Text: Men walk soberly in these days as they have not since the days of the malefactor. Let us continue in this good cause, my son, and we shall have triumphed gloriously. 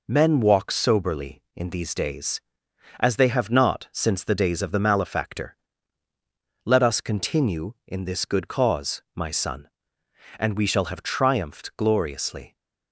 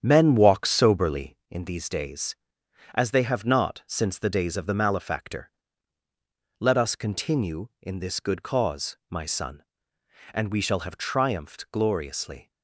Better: first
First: none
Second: starts louder than the rest; strong; until 1.5 s; 8.5 dB

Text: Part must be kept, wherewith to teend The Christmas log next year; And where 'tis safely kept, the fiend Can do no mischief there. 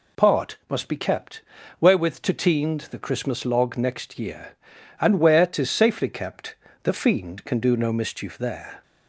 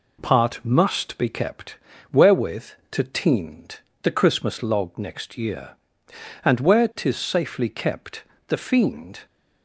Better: first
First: none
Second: pauses between "teend" and "The"; slight; at 3.7 s; 0.22 s long // stops before "Can do no mischief there"; at 9.2 s

